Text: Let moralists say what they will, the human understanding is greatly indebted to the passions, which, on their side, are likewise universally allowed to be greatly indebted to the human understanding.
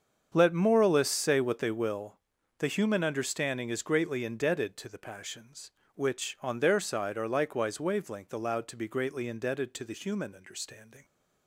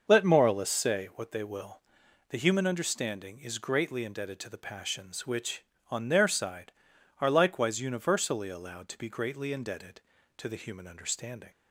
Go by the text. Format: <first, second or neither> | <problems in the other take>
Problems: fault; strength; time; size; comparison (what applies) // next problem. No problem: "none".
second | starts louder than the rest; strong; until 1.3 s; 7 dB; also in the second // says "wavelength" for "universally"; at 7.7 s